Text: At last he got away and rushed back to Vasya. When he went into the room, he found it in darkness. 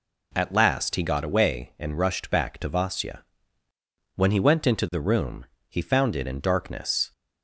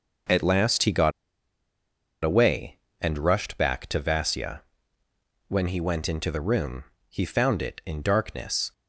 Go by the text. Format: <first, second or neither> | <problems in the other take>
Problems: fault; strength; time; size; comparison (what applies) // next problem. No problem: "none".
first | pauses between "got" and "away"; at 1.1 s; 1.1 s long